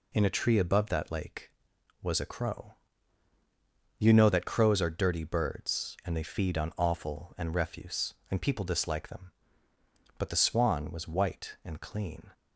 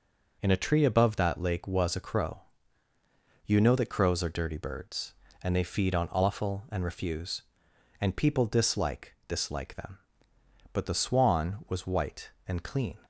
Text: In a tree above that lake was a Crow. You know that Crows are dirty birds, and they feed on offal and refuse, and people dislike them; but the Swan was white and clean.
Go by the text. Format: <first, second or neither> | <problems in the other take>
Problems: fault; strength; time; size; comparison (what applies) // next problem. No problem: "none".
first | says "dislike" twice; at 9.2 s